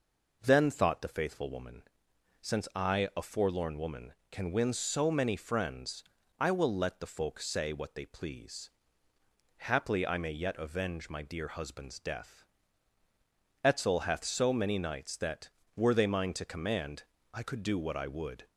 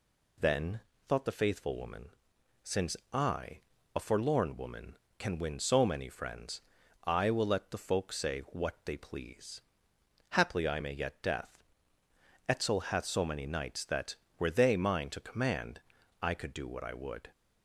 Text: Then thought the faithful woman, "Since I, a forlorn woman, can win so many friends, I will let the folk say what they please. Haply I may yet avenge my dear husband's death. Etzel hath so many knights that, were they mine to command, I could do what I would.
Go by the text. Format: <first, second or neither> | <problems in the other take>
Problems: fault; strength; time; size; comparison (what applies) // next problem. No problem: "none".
first | pauses between "Then" and "thought"; slight; at 0.8 s; 0.26 s long // pauses between "Since" and "I"; slight; at 2.9 s; 0.16 s long // skips "avenge my dear husband's"; at 11.2 s